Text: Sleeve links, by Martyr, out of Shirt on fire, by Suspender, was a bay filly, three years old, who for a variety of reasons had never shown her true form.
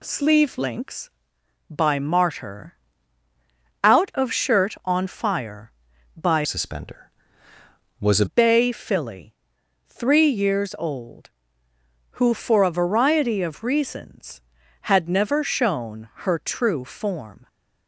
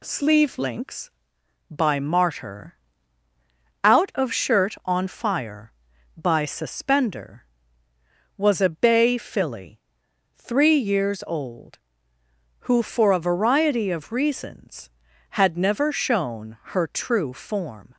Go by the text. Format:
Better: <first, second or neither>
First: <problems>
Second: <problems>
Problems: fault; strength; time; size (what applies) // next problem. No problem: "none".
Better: second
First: changes voice from "Suspender" to "a"; from 6.4 to 8.2 s; 1.8 s long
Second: none